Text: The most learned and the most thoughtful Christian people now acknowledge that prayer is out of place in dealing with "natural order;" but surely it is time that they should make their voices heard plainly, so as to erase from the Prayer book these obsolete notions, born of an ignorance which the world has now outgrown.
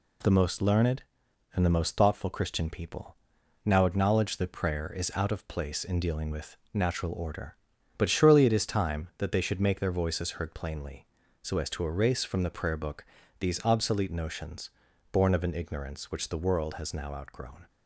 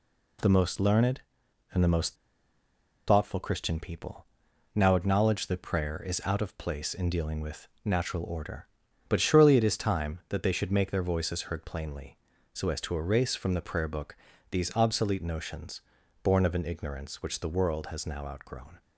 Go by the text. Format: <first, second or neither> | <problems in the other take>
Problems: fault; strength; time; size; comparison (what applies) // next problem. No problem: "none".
first | pauses between "most" and "thoughtful"; noticeable; at 2.1 s; 0.93 s long // pauses between "people" and "now"; noticeable; at 4.2 s; 0.50 s long; noticeable in the first // pauses between "with" and "natural"; slight; at 7.6 s; 0.16 s long; slight in the first // pauses between "book" and "these"; slight; at 14.1 s; 0.32 s long; slight in the first